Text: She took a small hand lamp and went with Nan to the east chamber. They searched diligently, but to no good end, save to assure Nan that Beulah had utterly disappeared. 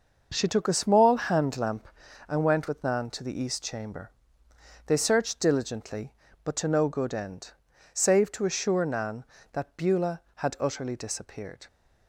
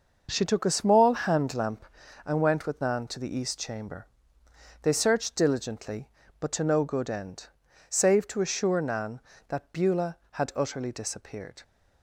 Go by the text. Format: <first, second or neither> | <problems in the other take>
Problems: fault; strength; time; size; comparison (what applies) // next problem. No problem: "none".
neither | none